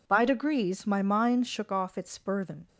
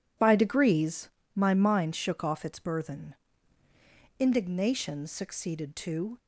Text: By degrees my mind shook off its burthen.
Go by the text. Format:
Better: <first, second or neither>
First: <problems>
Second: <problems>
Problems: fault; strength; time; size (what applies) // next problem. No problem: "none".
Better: first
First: none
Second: pauses between "degrees" and "my"; slight; at 1.0 s; 0.26 s long // goes on to say "Indignation succeeded to"; strong; from 4.1 s on; 2.0 s long